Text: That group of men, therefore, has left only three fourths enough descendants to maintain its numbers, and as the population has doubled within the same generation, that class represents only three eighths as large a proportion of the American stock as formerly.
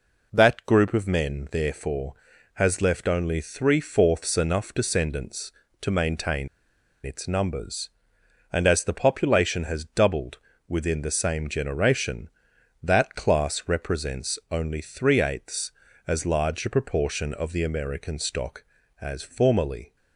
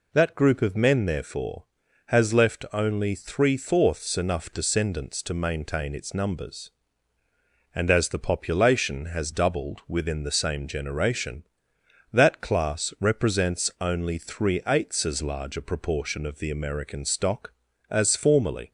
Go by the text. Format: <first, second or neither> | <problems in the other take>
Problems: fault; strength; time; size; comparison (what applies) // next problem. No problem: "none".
second | pauses between "maintain" and "its"; noticeable; at 6.4 s; 0.57 s long // pauses between "doubled" and "within"; slight; at 10.3 s; 0.30 s long